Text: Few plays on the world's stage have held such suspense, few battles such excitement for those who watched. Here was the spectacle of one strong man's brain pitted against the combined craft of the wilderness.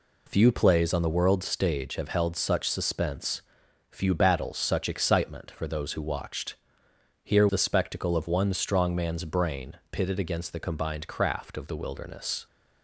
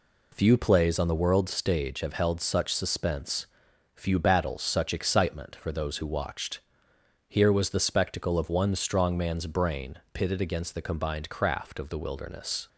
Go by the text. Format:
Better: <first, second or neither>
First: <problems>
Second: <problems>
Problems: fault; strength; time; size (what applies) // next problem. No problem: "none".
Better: second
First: skips "was"; at 7.4 s // pauses between "brain" and "pitted"; slight; at 9.7 s; 0.16 s long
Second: pauses between "brain" and "pitted"; slight; at 9.9 s; 0.16 s long